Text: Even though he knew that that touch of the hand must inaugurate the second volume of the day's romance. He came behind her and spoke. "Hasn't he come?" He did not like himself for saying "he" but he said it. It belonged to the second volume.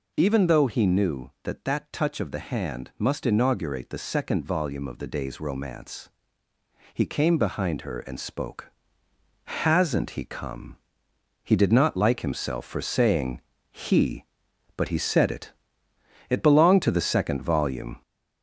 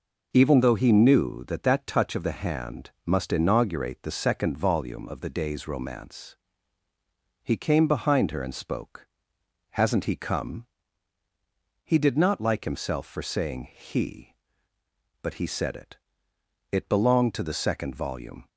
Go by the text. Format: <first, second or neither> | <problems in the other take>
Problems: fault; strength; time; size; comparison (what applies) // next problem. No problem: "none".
second | gets louder; noticeable; throughout; 4 dB // pauses between "saying" and "he"; slight; at 13.4 s; 0.30 s long